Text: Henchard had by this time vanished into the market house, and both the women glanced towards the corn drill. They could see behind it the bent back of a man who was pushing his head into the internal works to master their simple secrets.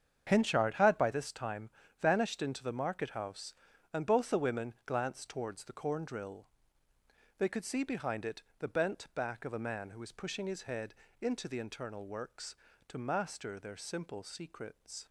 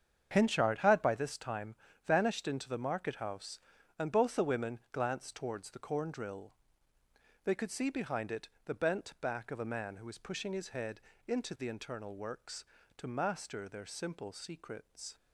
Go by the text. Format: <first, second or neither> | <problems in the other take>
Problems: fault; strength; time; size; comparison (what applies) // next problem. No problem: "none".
neither | starts louder than the rest; strong; the same in both // pauses between "time" and "vanished"; slight; the same in both // pauses between "it" and "the"; slight; the same in both // pauses between "head" and "into"; slight; the same in both